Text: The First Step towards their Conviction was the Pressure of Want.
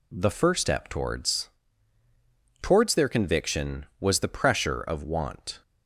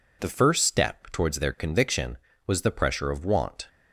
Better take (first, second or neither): second